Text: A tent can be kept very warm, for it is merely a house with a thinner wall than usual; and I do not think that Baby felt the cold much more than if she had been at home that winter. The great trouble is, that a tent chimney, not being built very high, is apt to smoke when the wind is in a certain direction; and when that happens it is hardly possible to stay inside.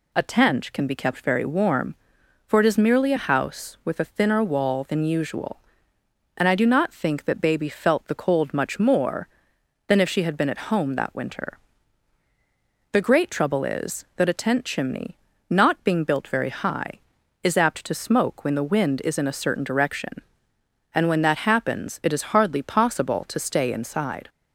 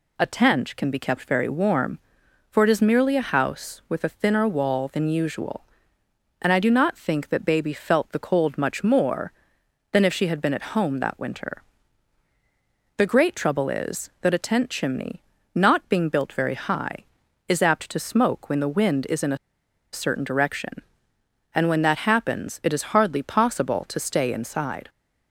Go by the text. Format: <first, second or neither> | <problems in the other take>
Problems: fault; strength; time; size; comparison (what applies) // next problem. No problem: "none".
first | pauses between "a" and "certain"; noticeable; at 19.3 s; 0.55 s long